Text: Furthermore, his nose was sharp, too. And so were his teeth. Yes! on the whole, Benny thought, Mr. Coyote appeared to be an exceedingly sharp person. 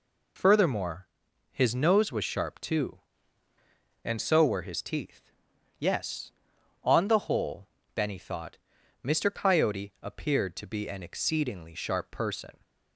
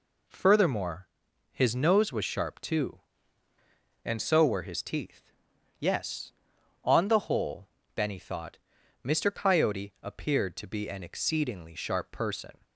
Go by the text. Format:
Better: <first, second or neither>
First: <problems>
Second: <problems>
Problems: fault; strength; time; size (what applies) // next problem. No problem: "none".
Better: second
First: loses the start of "Furthermore"; at 0.3 s; 75 ms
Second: none